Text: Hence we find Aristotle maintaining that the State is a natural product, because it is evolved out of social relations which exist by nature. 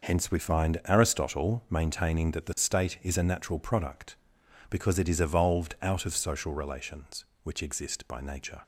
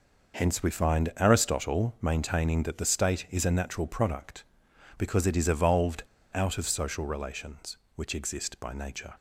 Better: first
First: none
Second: pauses between "evolved" and "out"; slight; at 6.0 s; 0.30 s long

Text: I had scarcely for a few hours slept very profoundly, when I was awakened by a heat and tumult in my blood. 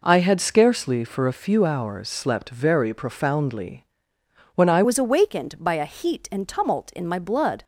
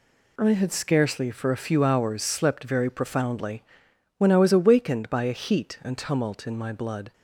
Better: second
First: changes voice at "was"; from 4.8 s on; 2.8 s long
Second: none

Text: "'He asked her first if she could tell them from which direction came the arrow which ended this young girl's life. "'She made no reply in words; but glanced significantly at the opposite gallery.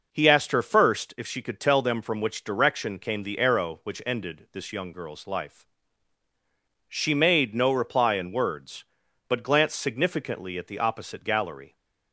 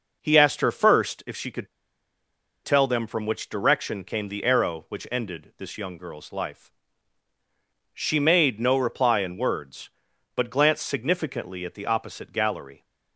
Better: first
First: none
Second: pauses between "could" and "tell"; noticeable; at 1.6 s; 0.96 s long

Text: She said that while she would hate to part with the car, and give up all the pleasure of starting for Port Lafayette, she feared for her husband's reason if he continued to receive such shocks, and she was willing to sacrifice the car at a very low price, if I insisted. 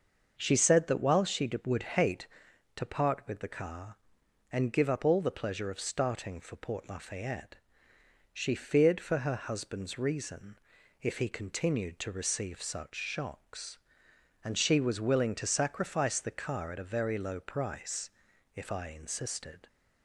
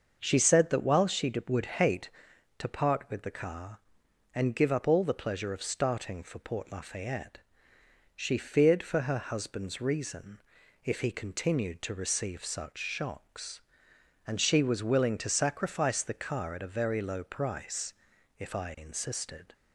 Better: neither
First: starts louder than the rest; until 1.4 s; 6.5 dB // pauses between "reason" and "if"; noticeable; at 10.5 s; 0.46 s long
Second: starts louder than the rest; until 1.2 s; 6.5 dB // pauses between "reason" and "if"; noticeable; at 10.3 s; 0.46 s long

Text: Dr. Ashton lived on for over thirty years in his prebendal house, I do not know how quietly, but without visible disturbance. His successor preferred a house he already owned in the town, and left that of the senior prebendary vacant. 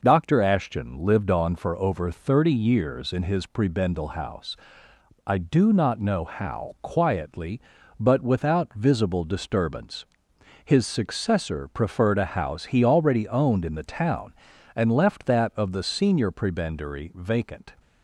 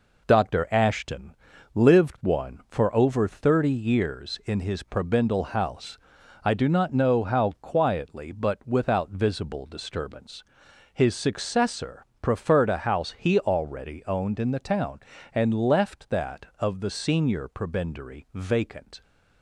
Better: first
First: none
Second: pauses between "Ashton" and "lived"; at 1.3 s; 0.38 s long // says "one" for "on"; at 2.2 s // pauses between "successor" and "preferred"; slight; at 12.0 s; 0.16 s long

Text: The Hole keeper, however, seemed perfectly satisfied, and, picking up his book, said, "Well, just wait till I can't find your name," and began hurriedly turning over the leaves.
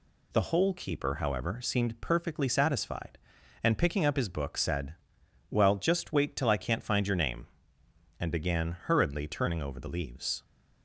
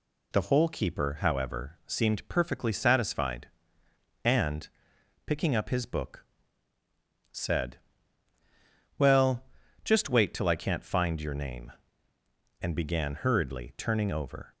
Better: first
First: none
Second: stops before "the leaves"; at 14.5 s

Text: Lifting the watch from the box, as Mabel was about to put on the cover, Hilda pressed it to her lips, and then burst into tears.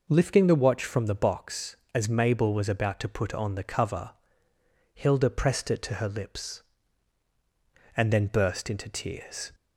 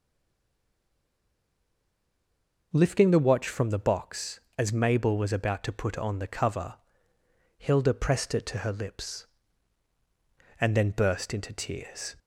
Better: first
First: none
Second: stays silent before the first word; strong; until 2.7 s; 2.7 s long

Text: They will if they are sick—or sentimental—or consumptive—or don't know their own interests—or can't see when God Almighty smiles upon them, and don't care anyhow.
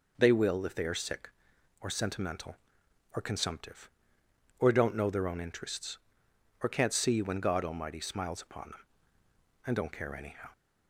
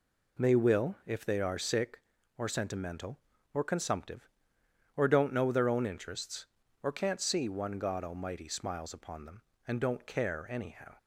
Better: first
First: none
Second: says "one" for "when"; at 7.4 s

